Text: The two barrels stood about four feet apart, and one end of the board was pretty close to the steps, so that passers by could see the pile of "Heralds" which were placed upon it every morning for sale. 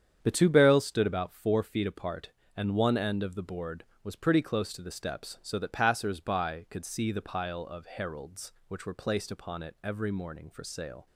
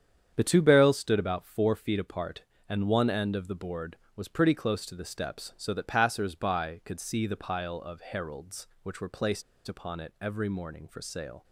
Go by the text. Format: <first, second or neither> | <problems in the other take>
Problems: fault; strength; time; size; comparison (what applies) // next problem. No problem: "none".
first | starts louder than the rest; strong; until 1.3 s; 8.5 dB; strong in the first // pauses between "placed" and "upon"; slight; at 9.4 s; 0.25 s long